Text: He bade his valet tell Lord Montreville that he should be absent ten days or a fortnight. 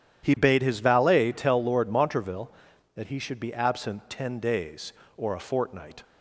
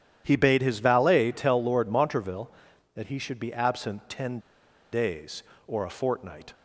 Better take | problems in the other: first | starts louder than the rest; strong; until 1.2 s; 10.5 dB; strong in the first // pauses between "ten" and "days"; noticeable; at 4.3 s; 0.52 s long

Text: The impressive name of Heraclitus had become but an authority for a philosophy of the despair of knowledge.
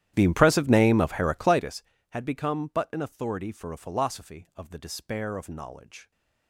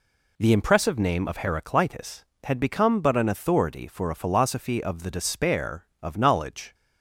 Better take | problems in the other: second | starts louder than the rest; strong; until 1.7 s; 12 dB

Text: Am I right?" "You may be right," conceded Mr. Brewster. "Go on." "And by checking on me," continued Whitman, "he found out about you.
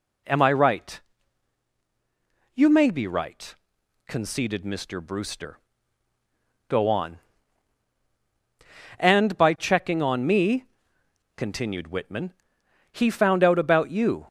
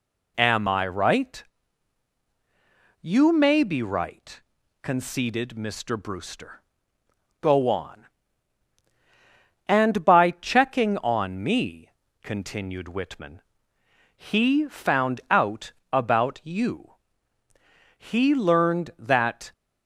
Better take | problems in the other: first | pauses between "out" and "about"; slight; at 15.7 s; 0.20 s long // goes on to say "He learned that"; from 17.9 s on; 1.5 s long

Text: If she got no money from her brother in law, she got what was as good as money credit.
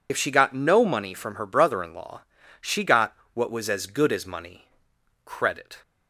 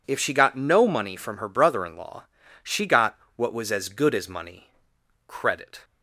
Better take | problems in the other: second | loses the start of "If"; at 0.0 s; 65 ms // pauses between "got" and "what"; slight; at 3.1 s; 0.20 s long; slight in the second // pauses between "money" and "credit"; noticeable; at 4.6 s; 0.58 s long; noticeable in the second

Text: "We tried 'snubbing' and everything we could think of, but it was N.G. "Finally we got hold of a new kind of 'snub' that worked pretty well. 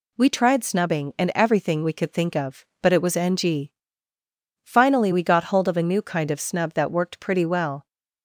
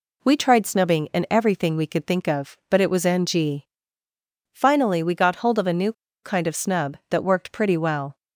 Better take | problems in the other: first | pauses between "new" and "kind"; slight; at 5.9 s; 0.29 s long

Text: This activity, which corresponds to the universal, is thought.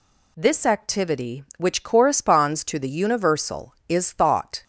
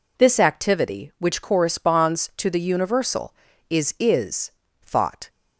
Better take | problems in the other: first | says "is" twice; at 3.9 s

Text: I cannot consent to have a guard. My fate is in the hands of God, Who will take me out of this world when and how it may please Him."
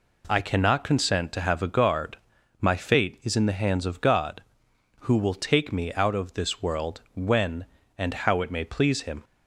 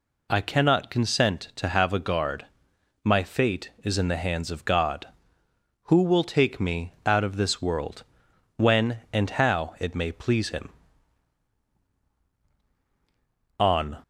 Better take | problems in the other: first | pauses between "world" and "when"; noticeable; at 8.0 s; 0.52 s long // goes on to say "On"; slight; from 13.5 s on; 0.40 s long

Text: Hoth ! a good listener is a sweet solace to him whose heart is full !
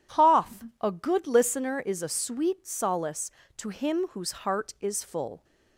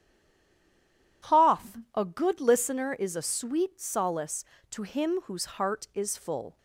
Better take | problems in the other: first | stays silent before the first word; noticeable; until 1.2 s; 1.2 s long

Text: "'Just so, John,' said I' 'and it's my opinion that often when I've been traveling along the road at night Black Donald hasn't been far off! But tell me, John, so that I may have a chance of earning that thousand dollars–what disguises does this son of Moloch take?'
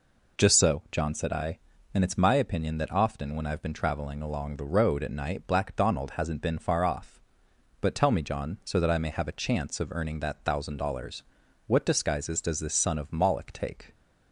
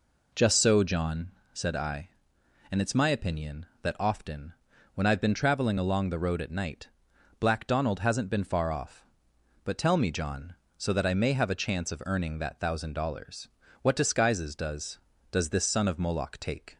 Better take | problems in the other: first | pauses between "often" and "when"; at 4.5 s; 0.40 s long // pauses between "night" and "Black"; noticeable; at 6.8 s; 0.54 s long // says "does" twice; at 15.3 s

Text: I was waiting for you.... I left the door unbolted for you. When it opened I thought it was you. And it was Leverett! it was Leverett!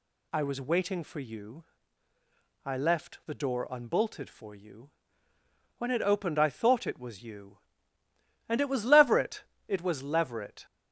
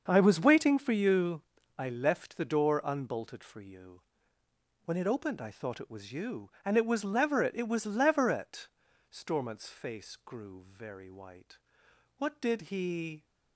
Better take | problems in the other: first | starts louder than the rest; until 1.0 s; 6.5 dB // goes on to say "Stormont's face grew very white What did he"; strong; from 9.1 s on; 4.1 s long

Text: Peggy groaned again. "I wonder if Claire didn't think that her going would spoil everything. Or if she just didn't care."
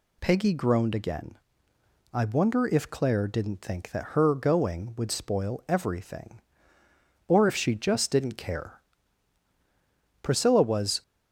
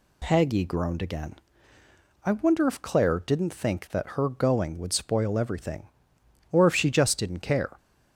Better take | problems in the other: second | goes on to say "Priscilla was"; noticeable; from 10.2 s on; 0.80 s long

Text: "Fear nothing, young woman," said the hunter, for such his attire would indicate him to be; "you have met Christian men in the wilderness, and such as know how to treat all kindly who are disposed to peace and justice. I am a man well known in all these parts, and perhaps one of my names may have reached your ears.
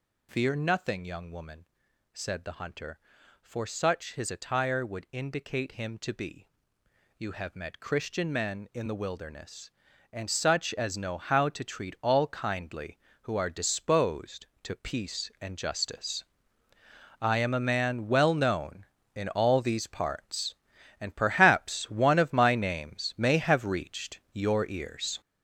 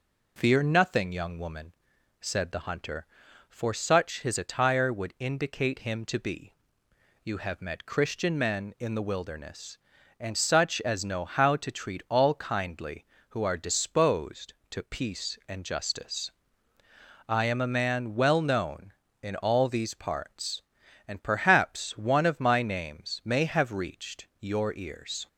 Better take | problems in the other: second | gets louder; strong; throughout; 8 dB

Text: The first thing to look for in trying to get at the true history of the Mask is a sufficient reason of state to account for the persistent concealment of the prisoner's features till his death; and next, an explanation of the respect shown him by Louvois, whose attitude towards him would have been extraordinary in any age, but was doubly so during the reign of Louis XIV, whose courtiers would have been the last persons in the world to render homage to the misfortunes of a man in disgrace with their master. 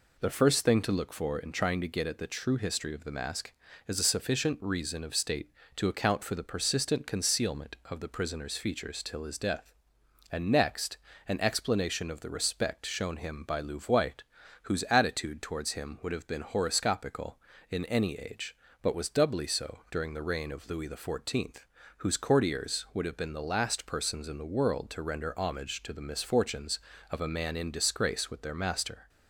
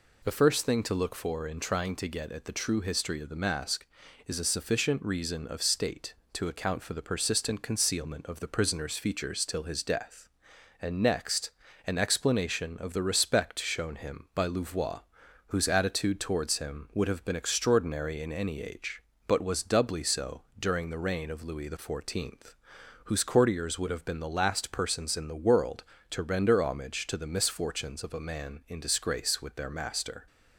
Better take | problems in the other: second | says "horoscopical" for "extraordinary"; at 16.4 s

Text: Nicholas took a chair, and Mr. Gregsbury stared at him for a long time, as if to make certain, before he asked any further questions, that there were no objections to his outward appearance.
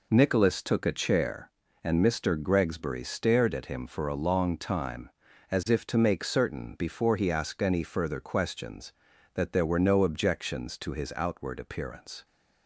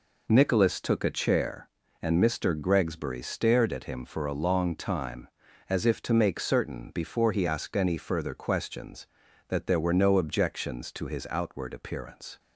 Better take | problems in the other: neither | none

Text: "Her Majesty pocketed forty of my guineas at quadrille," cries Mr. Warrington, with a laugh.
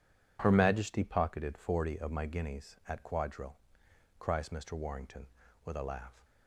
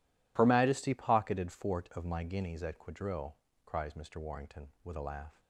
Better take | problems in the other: first | says "fort" for "forty"; at 1.5 s

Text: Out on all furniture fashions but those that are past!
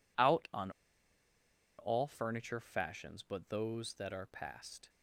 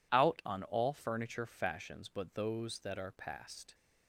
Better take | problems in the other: second | pauses between "on" and "all"; at 0.7 s; 1.0 s long

